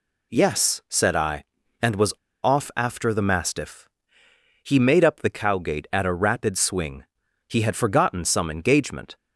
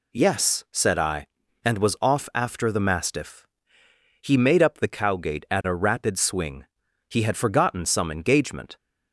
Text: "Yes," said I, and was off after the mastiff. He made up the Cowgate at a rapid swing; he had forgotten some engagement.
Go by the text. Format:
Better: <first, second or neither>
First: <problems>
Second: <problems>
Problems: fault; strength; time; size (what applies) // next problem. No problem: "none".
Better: second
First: pauses between "was" and "off"; slight; at 2.1 s; 0.28 s long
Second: none